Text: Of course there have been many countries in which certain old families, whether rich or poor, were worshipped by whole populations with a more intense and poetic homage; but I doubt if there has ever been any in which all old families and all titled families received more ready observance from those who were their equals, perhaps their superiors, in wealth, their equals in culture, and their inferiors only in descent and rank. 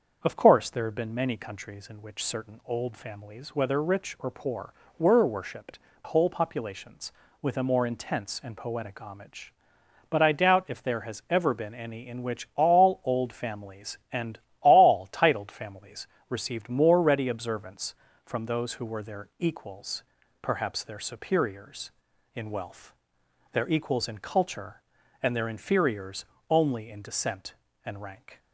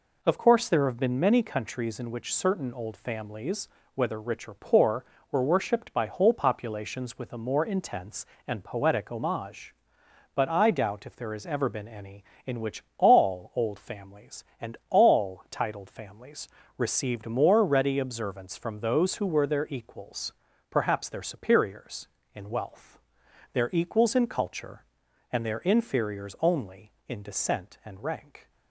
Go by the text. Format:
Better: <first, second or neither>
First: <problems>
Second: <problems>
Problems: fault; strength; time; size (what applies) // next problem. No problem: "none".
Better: second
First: starts louder than the rest; until 1.2 s; 6.5 dB // skips "by"; at 5.9 s // pauses between "and" and "all"; slight; at 14.3 s; 0.22 s long // pauses between "families" and "received"; slight; at 16.0 s; 0.22 s long // pauses between "inferiors" and "only"; slight; at 26.2 s; 0.24 s long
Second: pauses between "families" and "received"; slight; at 16.4 s; 0.30 s long